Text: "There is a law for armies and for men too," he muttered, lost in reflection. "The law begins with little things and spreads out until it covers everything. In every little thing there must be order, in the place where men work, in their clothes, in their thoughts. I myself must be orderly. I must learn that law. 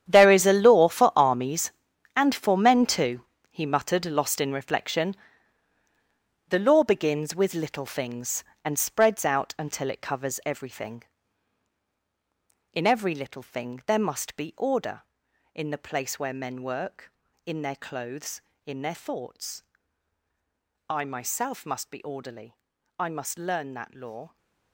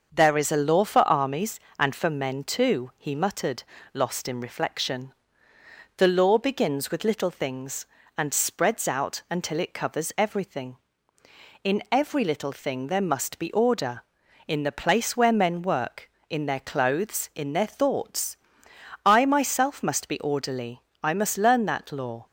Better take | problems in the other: second | gets quieter; strong; throughout; 15 dB // starts louder than the rest; strong; until 1.0 s; 9.5 dB; also in the second

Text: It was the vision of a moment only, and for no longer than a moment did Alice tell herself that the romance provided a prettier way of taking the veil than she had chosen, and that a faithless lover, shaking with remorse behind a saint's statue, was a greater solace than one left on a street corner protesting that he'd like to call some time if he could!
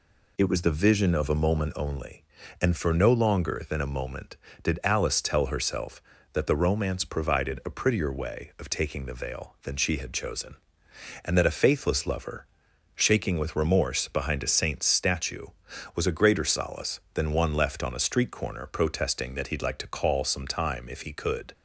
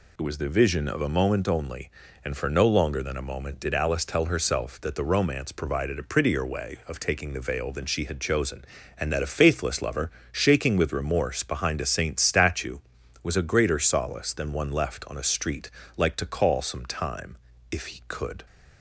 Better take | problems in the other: first | skips "corner protesting that he'd"; at 15.8 s // pauses between "time" and "if"; slight; at 17.3 s; 0.34 s long

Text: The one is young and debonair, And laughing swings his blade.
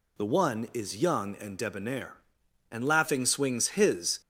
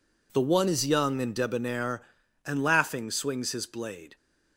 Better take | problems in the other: second | stops before "blade"; at 4.2 s

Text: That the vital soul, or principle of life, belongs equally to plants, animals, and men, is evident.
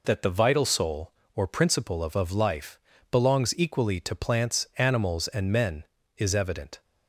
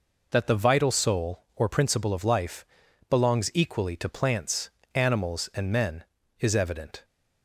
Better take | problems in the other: second | says "of" twice; at 2.1 s

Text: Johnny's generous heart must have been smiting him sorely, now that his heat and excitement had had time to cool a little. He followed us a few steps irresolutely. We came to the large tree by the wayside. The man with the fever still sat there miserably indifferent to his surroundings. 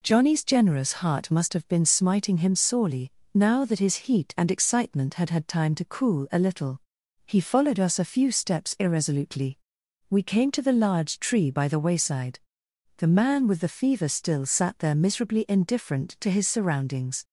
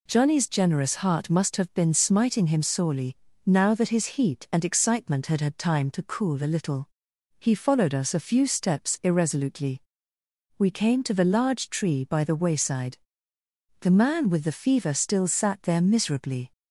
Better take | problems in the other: first | stops before "indifferent to his surroundings"; at 16.5 s

